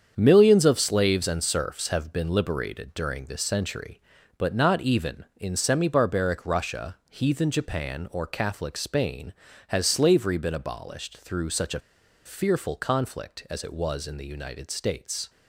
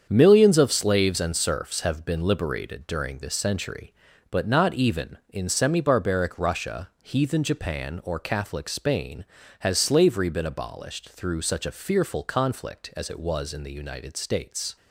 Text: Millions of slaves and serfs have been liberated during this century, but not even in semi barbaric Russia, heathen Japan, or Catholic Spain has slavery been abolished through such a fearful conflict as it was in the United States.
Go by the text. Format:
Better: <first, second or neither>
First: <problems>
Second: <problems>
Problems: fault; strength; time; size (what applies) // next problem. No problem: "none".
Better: second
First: starts louder than the rest; strong; until 1.1 s; 7.5 dB // pauses between "a" and "fearful"; at 11.8 s; 0.44 s long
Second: starts louder than the rest; strong; until 1.1 s; 7.5 dB